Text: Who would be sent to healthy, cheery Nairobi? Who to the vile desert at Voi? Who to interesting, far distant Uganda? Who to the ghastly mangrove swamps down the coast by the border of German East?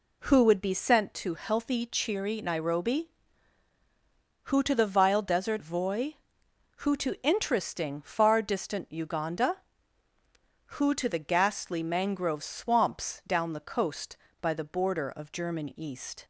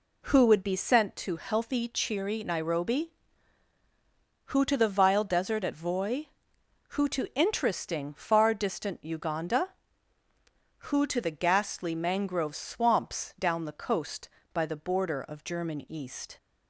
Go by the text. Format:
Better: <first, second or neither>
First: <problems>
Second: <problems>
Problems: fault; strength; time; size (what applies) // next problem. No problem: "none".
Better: second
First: skips "at"; at 5.6 s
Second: none